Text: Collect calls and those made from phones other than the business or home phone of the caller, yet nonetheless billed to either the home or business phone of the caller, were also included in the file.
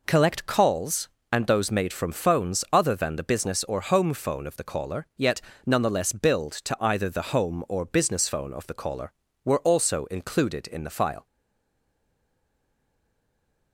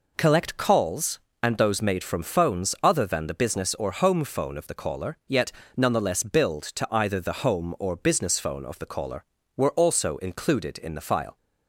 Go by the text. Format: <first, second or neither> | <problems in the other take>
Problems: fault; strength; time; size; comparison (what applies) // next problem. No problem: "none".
second | pauses between "yet" and "nonetheless"; slight; at 5.3 s; 0.26 s long; slight in the second // stays silent after the last word; from 11.2 s on; 2.5 s long